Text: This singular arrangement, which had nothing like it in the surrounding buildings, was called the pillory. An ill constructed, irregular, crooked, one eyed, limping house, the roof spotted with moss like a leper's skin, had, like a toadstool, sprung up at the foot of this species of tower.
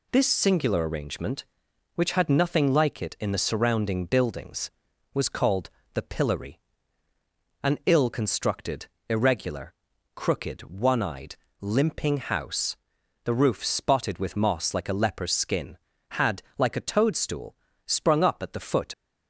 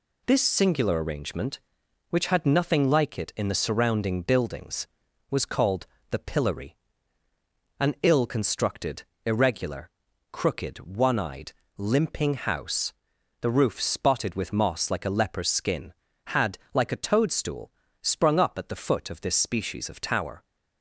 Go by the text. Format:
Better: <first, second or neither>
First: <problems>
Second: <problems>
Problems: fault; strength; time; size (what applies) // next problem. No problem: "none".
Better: second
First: pauses between "called" and "the"; slight; at 5.6 s; 0.26 s long // stops before "of this species of tower"; at 18.9 s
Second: pauses between "called" and "the"; slight; at 5.8 s; 0.26 s long